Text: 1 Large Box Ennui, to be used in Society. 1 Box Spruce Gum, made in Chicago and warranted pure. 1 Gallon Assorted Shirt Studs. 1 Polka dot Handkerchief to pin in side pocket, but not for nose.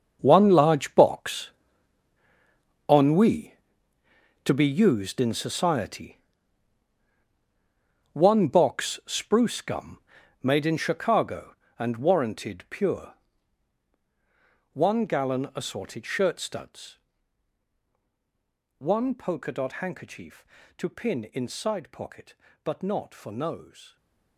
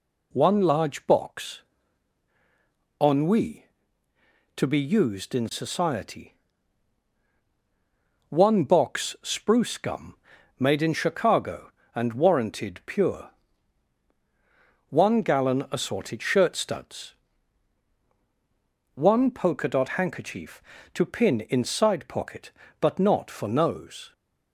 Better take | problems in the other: second | gets quieter; strong; throughout; 14 dB // pauses between "Box" and "Ennui"; strong; at 1.5 s; 1.3 s long; strong in the second // stays silent after the last word; slight; from 23.8 s on; 0.5 s long

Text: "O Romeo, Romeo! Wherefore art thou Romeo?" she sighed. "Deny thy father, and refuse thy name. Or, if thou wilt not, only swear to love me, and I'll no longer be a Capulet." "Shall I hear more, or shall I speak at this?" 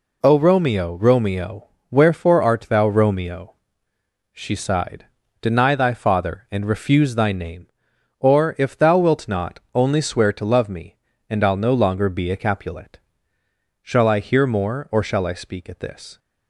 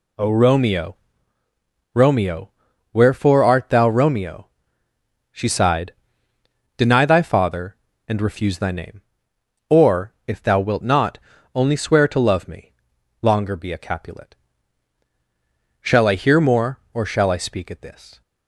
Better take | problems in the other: first | skips "and I'll no"; at 12.9 s

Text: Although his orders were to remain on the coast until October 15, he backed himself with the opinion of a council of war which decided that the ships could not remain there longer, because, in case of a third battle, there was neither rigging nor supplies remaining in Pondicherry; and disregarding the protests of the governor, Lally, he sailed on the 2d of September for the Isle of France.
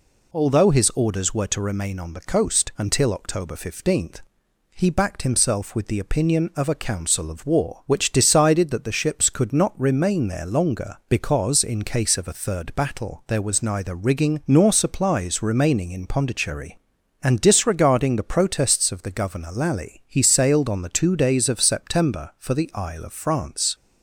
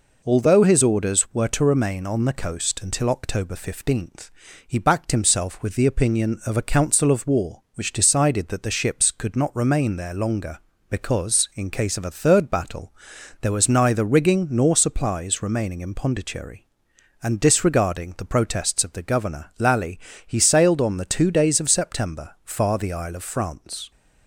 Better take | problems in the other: first | says "far" for "for"; at 22.4 s

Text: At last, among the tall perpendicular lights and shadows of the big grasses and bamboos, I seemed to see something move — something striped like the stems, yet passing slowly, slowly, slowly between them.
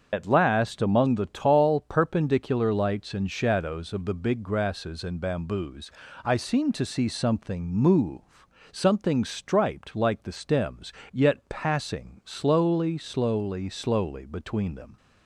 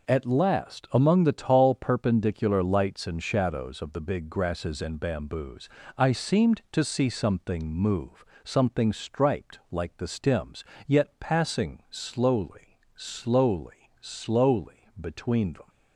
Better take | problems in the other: second | loses the start of "At"; at 0.1 s; 45 ms // starts louder than the rest; strong; until 1.1 s; 7 dB

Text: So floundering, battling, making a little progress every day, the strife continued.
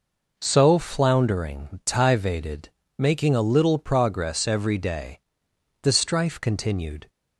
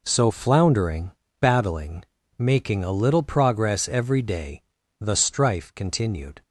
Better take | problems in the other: second | says "tivated" for "battling"; at 1.8 s

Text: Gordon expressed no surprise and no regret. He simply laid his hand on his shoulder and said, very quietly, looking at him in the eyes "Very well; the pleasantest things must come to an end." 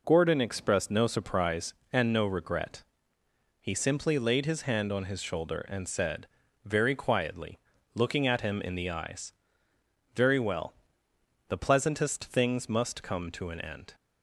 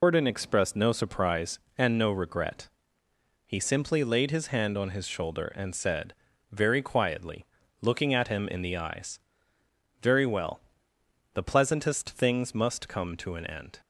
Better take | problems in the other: first | loses the start of "Gordon"; at 0.0 s; 105 ms // pauses between "eyes" and "Very"; noticeable; at 9.1 s; 0.86 s long; noticeable in the first

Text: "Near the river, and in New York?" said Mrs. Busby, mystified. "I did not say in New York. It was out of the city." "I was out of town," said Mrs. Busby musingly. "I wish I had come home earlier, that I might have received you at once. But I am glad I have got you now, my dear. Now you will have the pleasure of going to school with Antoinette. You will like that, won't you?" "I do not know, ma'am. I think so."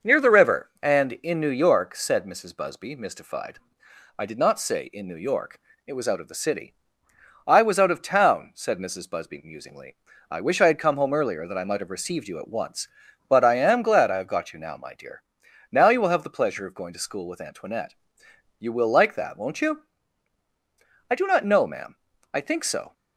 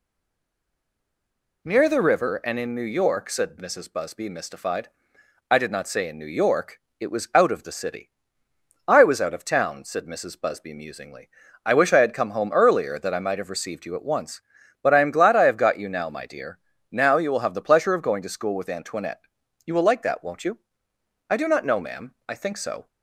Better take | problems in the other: first | stays silent before the first word; noticeable; until 1.6 s; 1.6 s long

